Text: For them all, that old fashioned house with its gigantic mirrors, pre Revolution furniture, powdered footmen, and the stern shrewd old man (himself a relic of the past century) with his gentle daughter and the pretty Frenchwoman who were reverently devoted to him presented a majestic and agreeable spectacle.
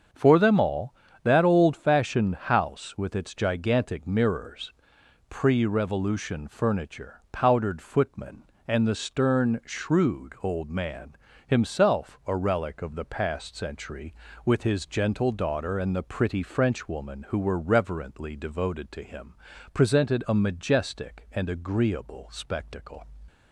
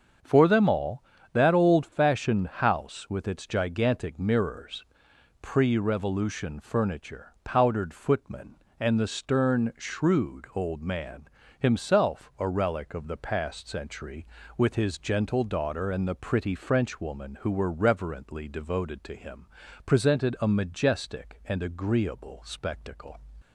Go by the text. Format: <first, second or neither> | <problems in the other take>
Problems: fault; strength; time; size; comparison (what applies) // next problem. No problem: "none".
neither | starts louder than the rest; the same in both // pauses between "him" and "presented"; the same in both